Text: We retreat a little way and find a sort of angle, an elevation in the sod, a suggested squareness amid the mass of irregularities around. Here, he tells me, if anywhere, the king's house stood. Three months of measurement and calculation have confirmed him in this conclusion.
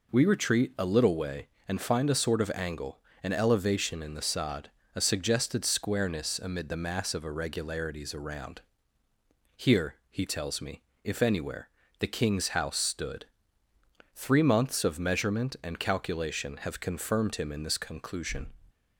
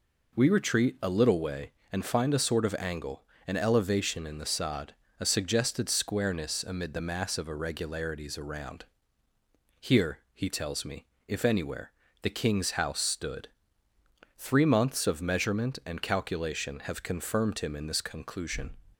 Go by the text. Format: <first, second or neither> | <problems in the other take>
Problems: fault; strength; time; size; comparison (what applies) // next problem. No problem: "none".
neither | none